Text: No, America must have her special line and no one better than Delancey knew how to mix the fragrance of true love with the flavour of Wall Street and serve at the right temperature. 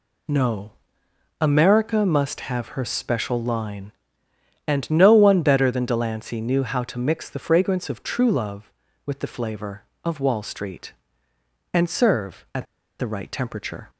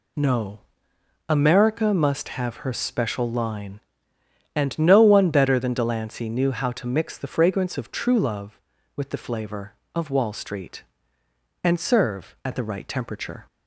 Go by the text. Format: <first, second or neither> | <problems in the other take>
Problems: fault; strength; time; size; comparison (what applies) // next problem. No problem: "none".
second | pauses between "at" and "the"; slight; at 12.6 s; 0.35 s long